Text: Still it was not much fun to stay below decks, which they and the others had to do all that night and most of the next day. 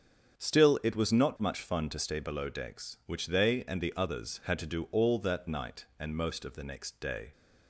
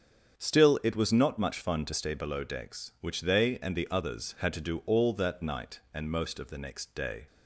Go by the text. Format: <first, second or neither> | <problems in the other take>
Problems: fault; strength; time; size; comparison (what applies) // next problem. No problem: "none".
neither | starts louder than the rest; strong; the same in both